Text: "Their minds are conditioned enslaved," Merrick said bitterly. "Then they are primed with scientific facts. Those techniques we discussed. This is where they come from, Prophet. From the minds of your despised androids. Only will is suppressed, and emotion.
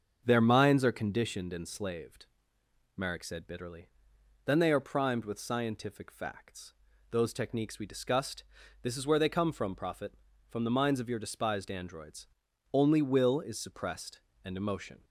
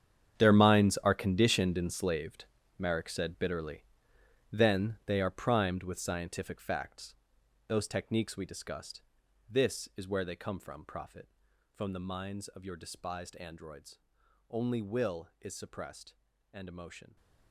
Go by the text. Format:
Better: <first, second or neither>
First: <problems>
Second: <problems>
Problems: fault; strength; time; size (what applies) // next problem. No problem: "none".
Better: first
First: starts louder than the rest; until 1.2 s; 7 dB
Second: gets quieter; strong; throughout; 15.5 dB // starts louder than the rest; strong; until 1.3 s; 8.5 dB